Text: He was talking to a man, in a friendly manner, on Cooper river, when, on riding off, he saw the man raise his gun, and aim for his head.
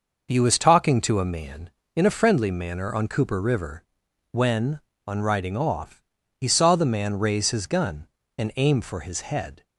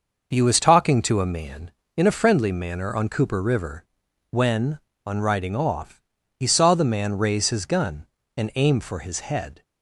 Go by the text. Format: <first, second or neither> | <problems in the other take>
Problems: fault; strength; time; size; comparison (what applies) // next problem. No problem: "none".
neither | none